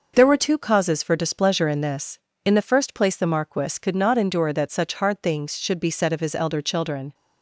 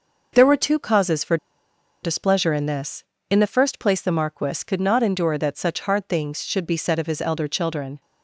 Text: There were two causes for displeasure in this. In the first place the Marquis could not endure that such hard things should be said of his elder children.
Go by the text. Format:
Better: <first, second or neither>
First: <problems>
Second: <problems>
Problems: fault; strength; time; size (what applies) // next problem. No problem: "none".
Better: first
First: none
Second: pauses between "for" and "displeasure"; noticeable; at 1.3 s; 0.67 s long